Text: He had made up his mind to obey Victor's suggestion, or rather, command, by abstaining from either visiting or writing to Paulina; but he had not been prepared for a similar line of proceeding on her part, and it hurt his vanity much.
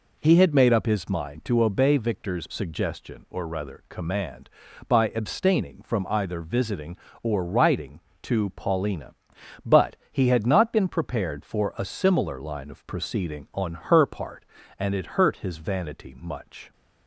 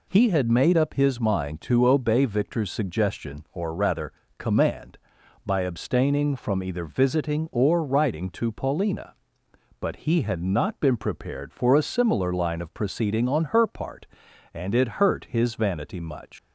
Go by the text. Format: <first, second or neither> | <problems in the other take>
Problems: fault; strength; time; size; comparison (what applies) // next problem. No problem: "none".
first | leaves "much" unfinished; at 16.3 s; 100 ms